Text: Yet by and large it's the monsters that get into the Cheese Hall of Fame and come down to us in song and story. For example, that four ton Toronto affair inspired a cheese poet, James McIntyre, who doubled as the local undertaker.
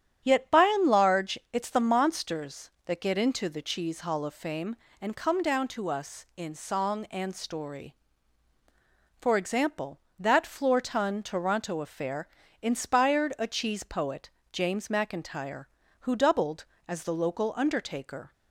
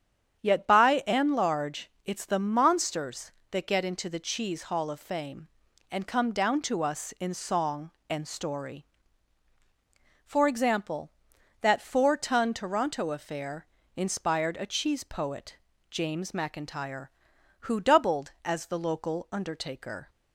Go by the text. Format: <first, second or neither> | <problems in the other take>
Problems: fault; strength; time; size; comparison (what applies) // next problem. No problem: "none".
second | starts louder than the rest; strong; until 1.2 s; 8.5 dB; strong in the second // pauses between "large" and "it's"; slight; at 1.3 s; 0.16 s long // says "floor" for "four"; at 10.4 s // pauses between "affair" and "inspired"; slight; at 12.2 s; 0.32 s long; slight in the second